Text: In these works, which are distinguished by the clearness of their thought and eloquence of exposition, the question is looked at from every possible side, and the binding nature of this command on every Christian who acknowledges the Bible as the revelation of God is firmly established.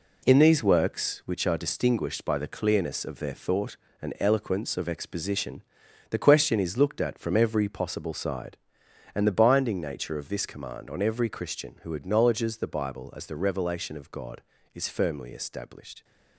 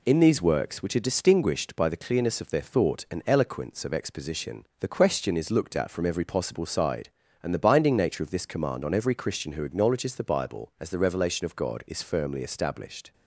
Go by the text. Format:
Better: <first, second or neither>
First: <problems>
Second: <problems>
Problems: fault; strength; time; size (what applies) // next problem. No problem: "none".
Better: second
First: gets quieter; strong; throughout; 7.5 dB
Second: none